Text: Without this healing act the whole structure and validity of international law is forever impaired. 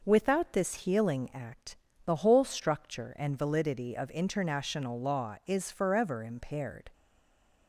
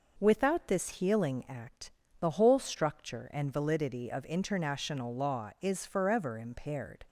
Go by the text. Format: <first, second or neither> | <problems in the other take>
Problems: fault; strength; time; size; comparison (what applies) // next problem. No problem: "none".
second | pauses between "act" and "the"; slight; at 1.7 s; 0.30 s long; slight in the second // stays silent after the last word; slight; from 6.9 s on; 0.7 s long